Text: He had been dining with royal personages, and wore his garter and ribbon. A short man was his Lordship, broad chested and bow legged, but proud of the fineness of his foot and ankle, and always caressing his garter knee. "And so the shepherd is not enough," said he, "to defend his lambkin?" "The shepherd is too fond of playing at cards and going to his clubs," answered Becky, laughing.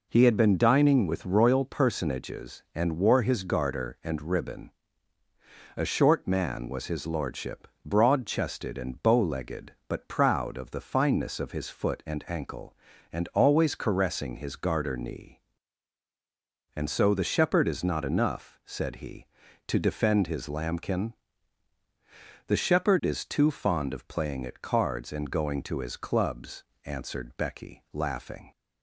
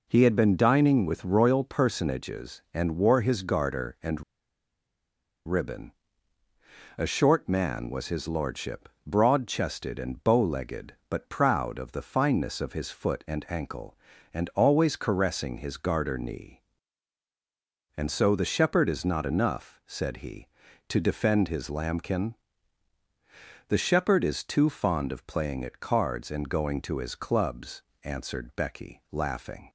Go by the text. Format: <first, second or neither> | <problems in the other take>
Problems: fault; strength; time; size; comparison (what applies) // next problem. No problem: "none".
first | pauses between "and" and "ribbon"; at 4.2 s; 1.2 s long